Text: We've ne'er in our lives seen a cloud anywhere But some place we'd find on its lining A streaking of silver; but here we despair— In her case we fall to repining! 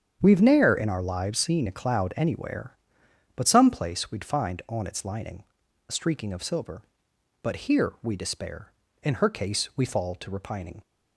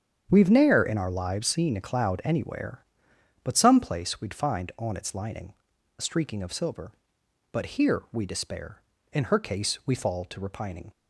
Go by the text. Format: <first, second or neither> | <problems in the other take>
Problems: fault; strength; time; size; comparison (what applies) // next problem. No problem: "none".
neither | starts louder than the rest; strong; the same in both // pauses between "lining" and "A"; the same in both